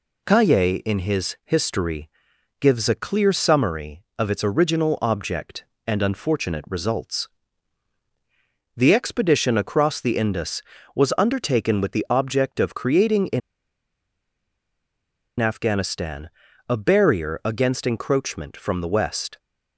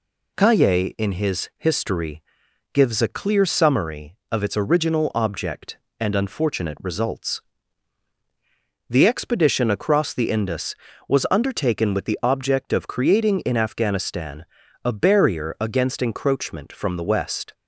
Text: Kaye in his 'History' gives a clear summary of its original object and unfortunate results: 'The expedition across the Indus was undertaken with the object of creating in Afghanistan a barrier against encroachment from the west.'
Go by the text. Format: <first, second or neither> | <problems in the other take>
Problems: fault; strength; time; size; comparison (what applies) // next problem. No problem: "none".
second | pauses between "History" and "gives"; noticeable; at 2.0 s; 0.52 s long; noticeable in the second // pauses between "in" and "Afghanistan"; strong; at 13.4 s; 2.0 s long // pauses between "Afghanistan" and "a"; at 16.2 s; 0.40 s long; also in the second